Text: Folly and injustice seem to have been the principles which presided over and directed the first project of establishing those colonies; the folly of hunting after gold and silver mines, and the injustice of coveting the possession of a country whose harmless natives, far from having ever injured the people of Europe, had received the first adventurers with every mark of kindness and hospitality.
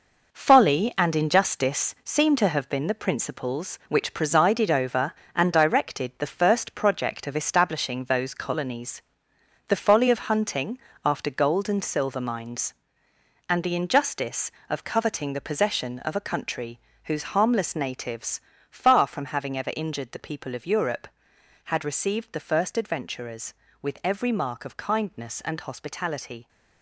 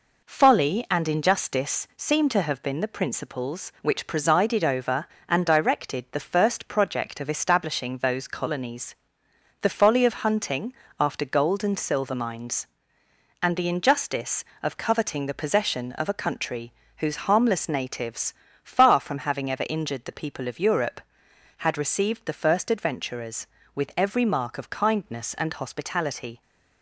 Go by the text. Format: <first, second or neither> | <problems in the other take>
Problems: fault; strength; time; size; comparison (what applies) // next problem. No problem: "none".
second | gets quieter; strong; throughout; 8 dB // pauses between "hunting" and "after"; slight; at 10.7 s; 0.26 s long; slight in the second // pauses between "country" and "whose"; slight; at 16.7 s; 0.26 s long; slight in the second